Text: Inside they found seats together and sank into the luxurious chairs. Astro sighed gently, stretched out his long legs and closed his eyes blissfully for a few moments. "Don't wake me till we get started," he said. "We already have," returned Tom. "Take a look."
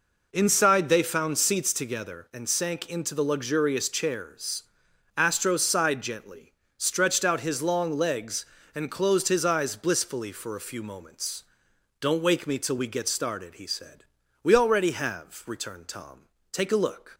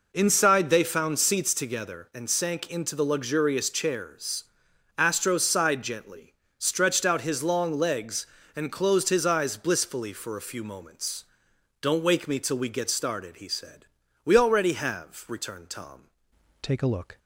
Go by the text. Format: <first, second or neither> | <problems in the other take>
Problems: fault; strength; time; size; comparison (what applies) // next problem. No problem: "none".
first | changes voice at "Take"; from 16.6 s on; 0.5 s long